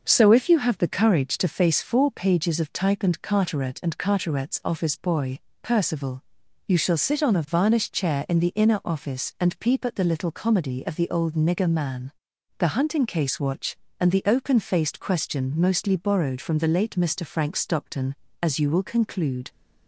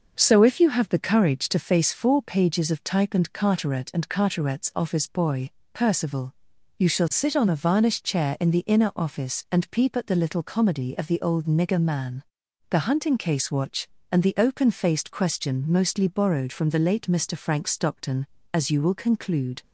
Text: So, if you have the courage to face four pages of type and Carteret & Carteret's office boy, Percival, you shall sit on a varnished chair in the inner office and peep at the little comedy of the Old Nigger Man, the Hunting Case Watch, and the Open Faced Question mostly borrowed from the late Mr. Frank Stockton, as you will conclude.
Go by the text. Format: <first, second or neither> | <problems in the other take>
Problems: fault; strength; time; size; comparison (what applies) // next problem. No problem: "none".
neither | starts louder than the rest; the same in both